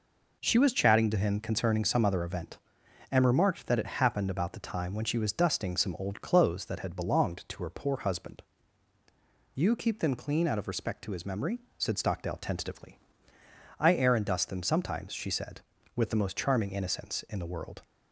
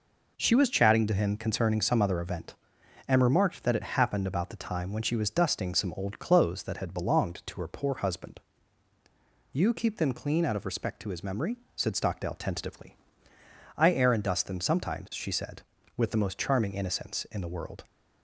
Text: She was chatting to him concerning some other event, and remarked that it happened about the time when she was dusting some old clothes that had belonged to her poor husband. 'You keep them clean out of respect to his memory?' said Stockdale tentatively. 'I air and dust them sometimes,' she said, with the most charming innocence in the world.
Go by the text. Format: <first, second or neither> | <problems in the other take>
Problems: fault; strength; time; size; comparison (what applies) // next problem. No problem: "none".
neither | none